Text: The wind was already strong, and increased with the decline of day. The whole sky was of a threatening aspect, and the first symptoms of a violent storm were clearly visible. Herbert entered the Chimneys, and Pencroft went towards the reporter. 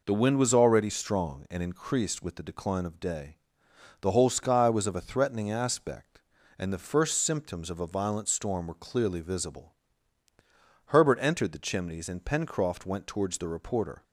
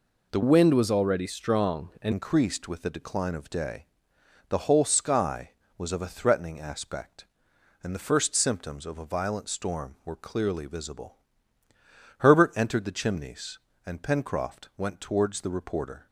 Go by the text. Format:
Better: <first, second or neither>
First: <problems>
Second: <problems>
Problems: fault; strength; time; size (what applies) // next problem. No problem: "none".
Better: first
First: none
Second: changes voice from "wind" to "and"; from 0.4 to 2.1 s; 1.7 s long